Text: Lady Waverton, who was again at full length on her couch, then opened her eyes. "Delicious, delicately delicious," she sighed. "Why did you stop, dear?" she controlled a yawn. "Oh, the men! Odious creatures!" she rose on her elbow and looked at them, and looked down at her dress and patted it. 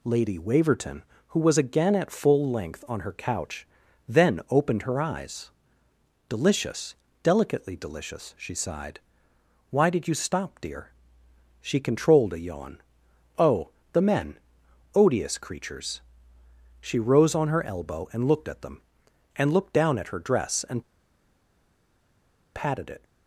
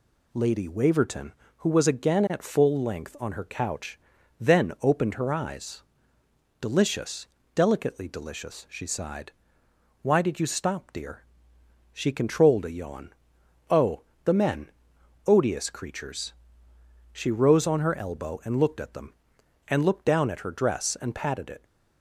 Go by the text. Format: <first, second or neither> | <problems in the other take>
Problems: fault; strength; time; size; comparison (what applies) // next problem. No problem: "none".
second | pauses between "and" and "patted"; strong; at 20.8 s; 1.7 s long